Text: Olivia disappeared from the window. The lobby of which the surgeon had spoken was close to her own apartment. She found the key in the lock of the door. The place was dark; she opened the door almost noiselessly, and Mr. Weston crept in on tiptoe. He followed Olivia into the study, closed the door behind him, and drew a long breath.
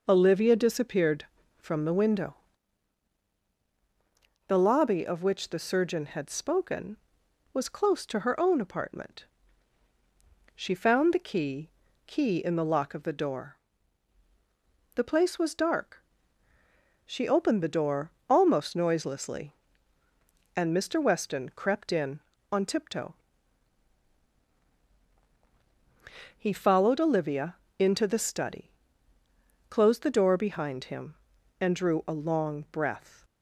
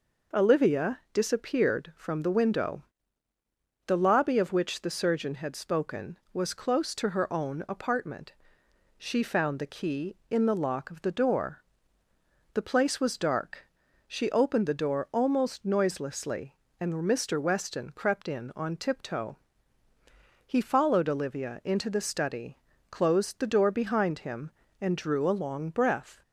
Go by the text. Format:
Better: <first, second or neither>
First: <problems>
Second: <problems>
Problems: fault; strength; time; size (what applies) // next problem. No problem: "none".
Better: second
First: says "key" twice; at 12.0 s // pauses between "door" and "almost"; slight; at 18.1 s; 0.18 s long // pauses between "Olivia" and "into"; slight; at 27.5 s; 0.24 s long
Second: none